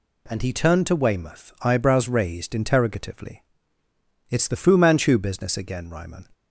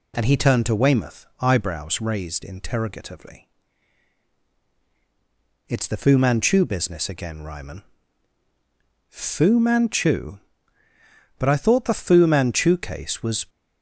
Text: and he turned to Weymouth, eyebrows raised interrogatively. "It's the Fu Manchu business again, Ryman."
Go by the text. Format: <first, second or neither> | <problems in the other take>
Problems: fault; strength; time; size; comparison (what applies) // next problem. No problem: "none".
first | goes on to say "Fu Manchu But I thought the Fu Manchu case was"; strong; from 9.0 s on; 4.3 s long